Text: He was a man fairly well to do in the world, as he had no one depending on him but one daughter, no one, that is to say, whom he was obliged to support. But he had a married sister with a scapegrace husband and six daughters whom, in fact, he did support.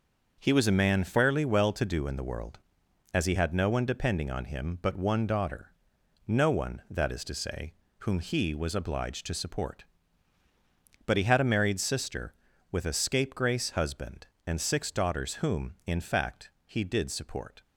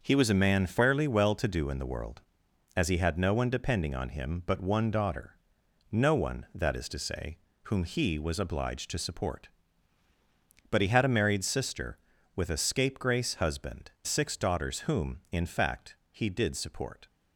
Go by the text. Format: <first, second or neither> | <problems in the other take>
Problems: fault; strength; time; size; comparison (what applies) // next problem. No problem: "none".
first | starts louder than the rest; noticeable; until 1.0 s; 6 dB; noticeable in the first // skips "and"; at 13.9 s